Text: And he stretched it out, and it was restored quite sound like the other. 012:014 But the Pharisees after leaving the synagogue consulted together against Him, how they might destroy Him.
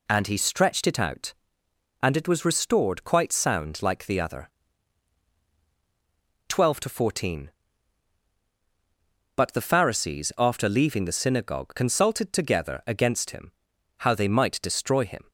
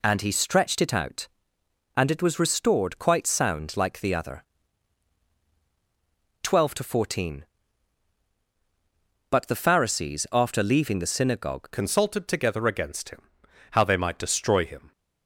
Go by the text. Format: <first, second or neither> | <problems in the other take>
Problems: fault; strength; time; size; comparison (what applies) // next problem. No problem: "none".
first | changes voice at "consulted"; from 11.7 s on; 3.2 s long